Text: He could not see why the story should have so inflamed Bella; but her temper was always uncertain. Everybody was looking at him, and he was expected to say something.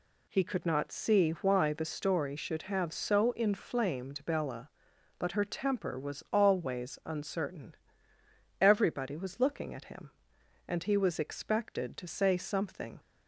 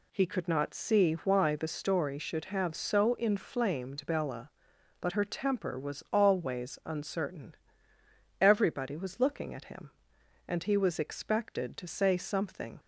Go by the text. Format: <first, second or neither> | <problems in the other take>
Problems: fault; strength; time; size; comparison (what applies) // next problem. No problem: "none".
neither | none